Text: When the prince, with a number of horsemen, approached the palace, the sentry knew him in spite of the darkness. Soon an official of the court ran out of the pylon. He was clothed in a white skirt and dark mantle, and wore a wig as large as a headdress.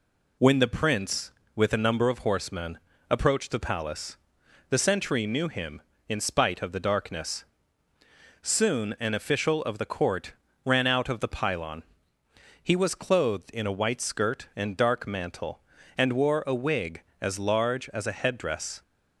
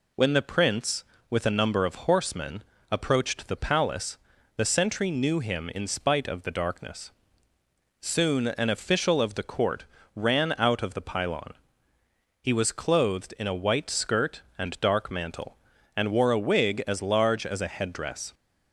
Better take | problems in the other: neither | pauses between "court" and "ran"; slight; the same in both

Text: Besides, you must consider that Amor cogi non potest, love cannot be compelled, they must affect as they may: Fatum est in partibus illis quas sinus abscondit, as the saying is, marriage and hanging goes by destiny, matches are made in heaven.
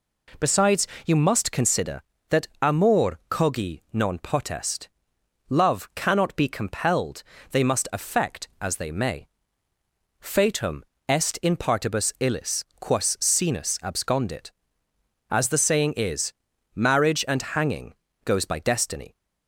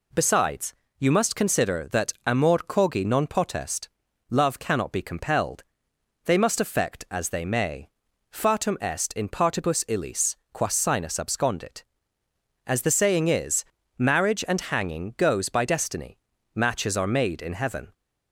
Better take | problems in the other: second | pauses between "Fatum" and "est"; slight; at 10.8 s; 0.25 s long // pauses between "illis" and "quas"; slight; at 12.6 s; 0.16 s long; slight in the second // pauses between "hanging" and "goes"; slight; at 17.9 s; 0.32 s long // stops before "matches are made in heaven"; at 19.1 s

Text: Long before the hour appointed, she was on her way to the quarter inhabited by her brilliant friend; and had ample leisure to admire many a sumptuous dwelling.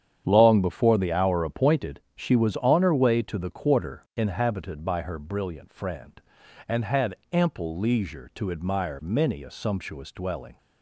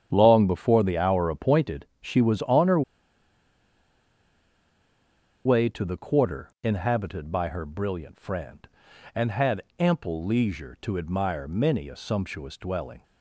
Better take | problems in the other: first | starts louder than the rest; strong; until 1.1 s; 9 dB; strong in the first // pauses between "her" and "way"; strong; at 2.8 s; 2.6 s long // pauses between "had" and "ample"; slight; at 9.6 s; 0.16 s long; slight in the first

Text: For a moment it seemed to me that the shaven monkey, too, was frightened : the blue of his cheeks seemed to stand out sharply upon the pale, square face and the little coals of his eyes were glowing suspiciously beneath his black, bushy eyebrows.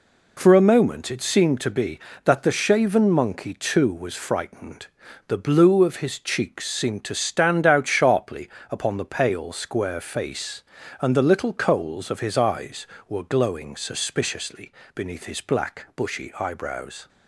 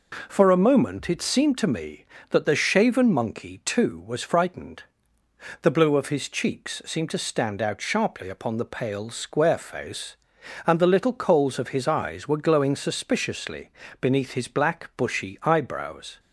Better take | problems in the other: second | says "be" for "me"; at 1.6 s // pauses between "sharply" and "upon"; slight; at 8.4 s; 0.22 s long // pauses between "suspiciously" and "beneath"; slight; at 14.6 s; 0.24 s long; slight in the second

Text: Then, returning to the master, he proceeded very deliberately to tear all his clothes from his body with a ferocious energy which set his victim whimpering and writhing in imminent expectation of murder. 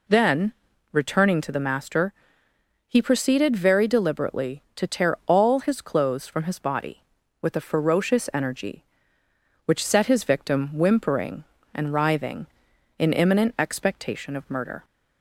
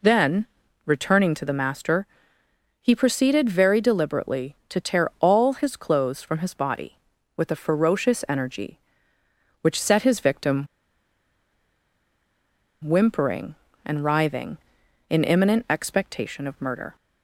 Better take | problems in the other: first | pauses between "victim" and "whimpering"; strong; at 10.6 s; 2.1 s long

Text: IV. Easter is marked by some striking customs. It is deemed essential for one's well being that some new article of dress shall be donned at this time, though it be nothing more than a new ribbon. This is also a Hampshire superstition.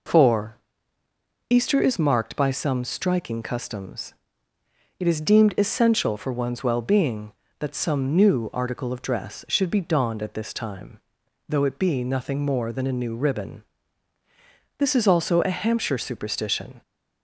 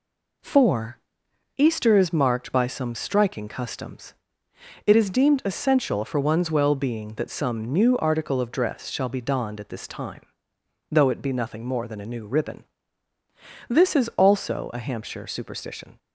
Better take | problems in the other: second | says "should" for "shall"; at 9.4 s

